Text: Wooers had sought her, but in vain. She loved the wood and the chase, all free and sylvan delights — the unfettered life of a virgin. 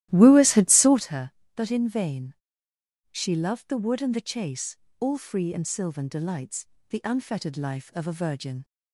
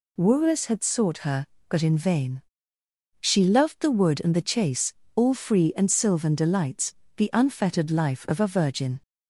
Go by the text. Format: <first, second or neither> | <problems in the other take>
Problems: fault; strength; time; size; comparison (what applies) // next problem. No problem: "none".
second | starts louder than the rest; strong; until 1.1 s; 14.5 dB